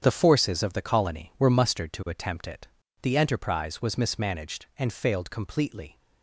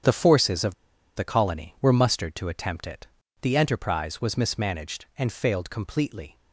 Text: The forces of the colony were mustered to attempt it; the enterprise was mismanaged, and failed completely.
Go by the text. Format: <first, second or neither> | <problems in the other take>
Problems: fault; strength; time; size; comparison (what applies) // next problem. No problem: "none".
first | starts louder than the rest; strong; until 1.4 s; 8 dB; strong in the first // pauses between "of" and "the"; at 0.7 s; 0.41 s long